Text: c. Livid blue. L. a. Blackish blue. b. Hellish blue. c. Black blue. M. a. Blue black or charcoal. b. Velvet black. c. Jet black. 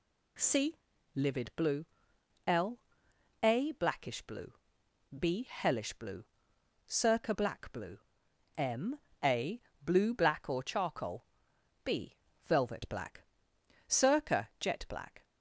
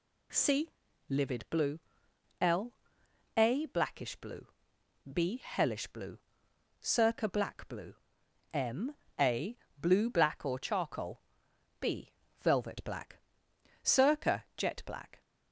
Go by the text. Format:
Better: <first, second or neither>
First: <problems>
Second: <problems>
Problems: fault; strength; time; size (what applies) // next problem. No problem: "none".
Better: neither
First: none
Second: none